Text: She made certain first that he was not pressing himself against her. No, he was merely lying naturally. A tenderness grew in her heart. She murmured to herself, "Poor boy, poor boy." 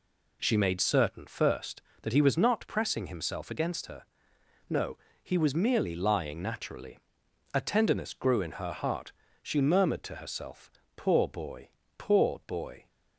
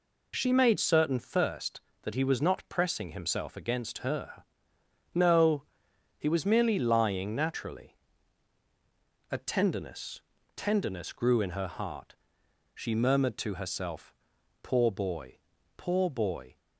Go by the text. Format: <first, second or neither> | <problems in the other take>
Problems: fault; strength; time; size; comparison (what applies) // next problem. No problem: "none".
first | says "tenderness" twice; at 10.5 s